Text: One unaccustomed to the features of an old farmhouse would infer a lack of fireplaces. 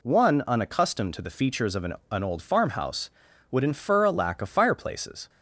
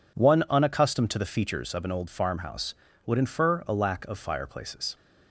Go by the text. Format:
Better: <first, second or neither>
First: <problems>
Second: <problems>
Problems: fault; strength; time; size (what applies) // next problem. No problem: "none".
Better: second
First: says "an" twice; at 2.1 s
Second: none